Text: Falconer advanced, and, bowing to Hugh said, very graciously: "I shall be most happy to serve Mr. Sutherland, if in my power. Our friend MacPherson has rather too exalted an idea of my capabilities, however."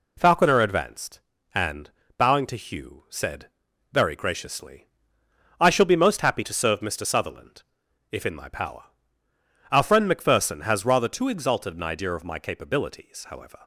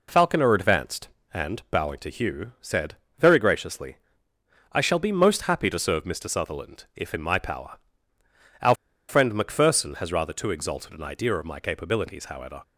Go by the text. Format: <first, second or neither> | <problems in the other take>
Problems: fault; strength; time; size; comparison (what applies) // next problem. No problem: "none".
first | pauses between "Our" and "friend"; slight; at 8.7 s; 0.35 s long